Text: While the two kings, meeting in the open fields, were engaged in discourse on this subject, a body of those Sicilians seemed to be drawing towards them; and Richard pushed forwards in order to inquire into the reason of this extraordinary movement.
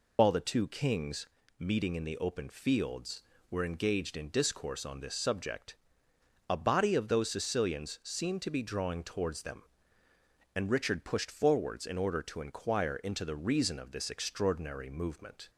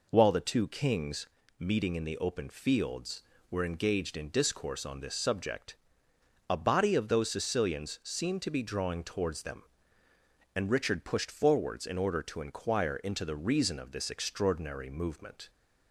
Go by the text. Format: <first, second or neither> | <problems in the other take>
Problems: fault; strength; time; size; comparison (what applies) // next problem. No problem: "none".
second | loses the start of "While"; at 0.1 s; 95 ms